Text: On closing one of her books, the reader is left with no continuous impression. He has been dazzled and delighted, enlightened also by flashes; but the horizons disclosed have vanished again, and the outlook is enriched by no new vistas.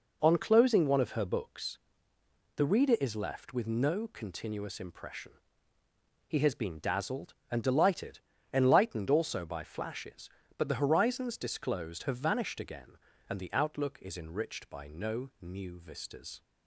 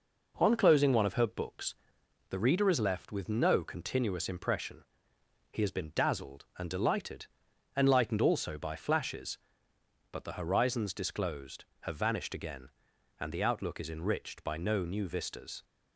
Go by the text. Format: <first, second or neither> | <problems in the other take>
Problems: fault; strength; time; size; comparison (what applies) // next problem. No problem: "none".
neither | none